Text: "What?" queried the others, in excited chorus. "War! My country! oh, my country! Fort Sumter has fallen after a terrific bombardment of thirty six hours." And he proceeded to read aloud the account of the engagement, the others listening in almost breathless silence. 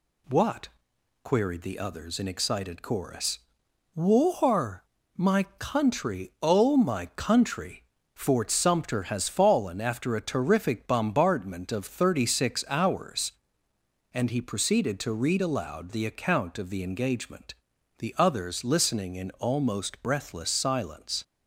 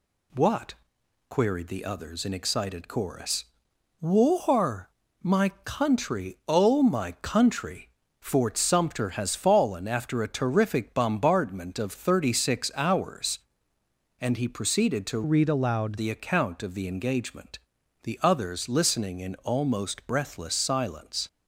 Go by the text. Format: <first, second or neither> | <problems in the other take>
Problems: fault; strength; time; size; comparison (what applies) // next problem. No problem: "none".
first | pauses between "My" and "country"; slight; at 5.4 s; 0.16 s long; slight in the first // pauses between "my" and "country"; slight; at 7.1 s; 0.22 s long; slight in the first // changes voice from "read" to "aloud"; from 15.2 to 15.9 s; 0.7 s long